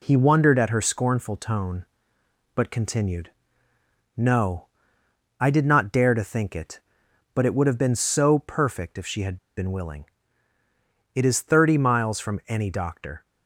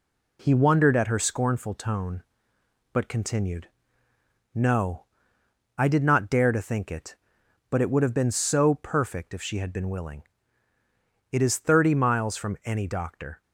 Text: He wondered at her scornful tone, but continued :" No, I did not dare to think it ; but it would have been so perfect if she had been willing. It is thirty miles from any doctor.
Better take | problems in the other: second | pauses between "had" and "been"; slight; at 9.3 s; 0.20 s long

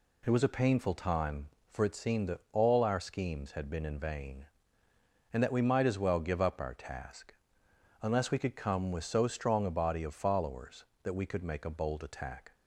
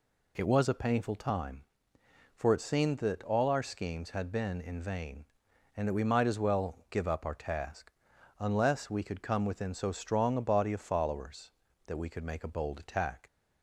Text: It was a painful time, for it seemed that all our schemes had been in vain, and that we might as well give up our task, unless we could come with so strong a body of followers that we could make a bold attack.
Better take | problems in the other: first | says "within" for "with"; at 9.4 s

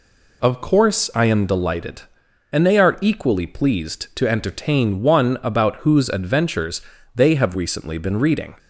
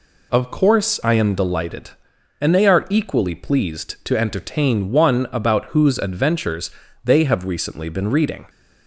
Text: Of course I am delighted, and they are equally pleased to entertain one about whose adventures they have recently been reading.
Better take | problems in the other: neither | pauses between "adventures" and "they"; slight; the same in both

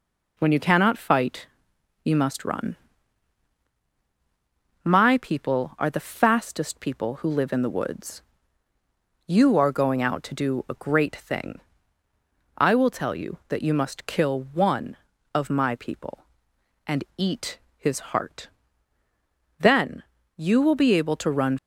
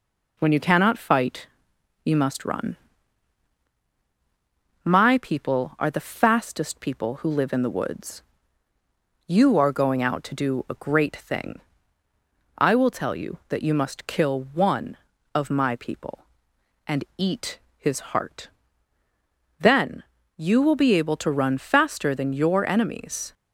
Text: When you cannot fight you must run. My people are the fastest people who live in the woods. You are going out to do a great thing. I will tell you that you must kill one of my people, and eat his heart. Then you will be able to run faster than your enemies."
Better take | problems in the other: second | pauses between "fight" and "you"; noticeable; at 1.4 s; 0.56 s long; noticeable in the second // pauses between "eat" and "his"; slight; at 17.5 s; 0.18 s long; slight in the second // pauses between "Then" and "you"; slight; at 20.0 s; 0.34 s long; slight in the second // stops before "faster than your enemies"; at 21.5 s

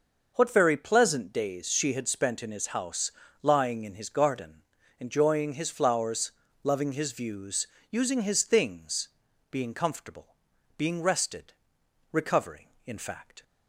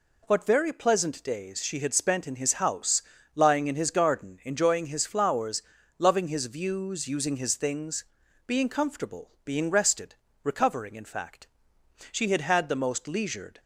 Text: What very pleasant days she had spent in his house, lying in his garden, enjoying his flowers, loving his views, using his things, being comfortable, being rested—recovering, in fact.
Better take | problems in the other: first | goes on to say "She had had the most leisured"; from 12.0 s on; 1.5 s long

